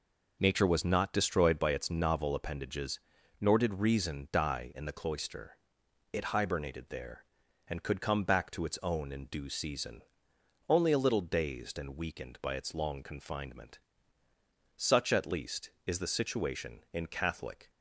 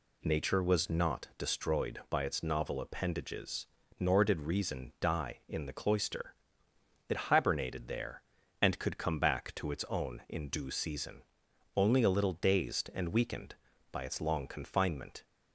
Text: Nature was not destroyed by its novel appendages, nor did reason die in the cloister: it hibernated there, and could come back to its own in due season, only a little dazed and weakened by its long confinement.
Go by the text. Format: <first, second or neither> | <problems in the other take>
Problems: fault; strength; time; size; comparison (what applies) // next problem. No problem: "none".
second | goes on to say "Such at least is the situation in Catholic"; strong; from 14.7 s on; 2.9 s long